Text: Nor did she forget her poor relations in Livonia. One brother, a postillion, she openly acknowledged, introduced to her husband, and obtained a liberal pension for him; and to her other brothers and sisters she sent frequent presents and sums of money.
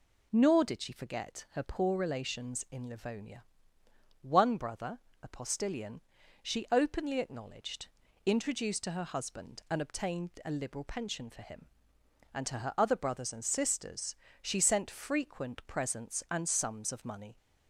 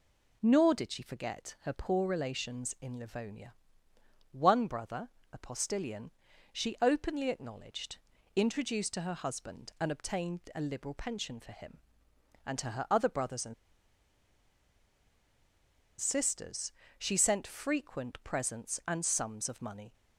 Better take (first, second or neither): first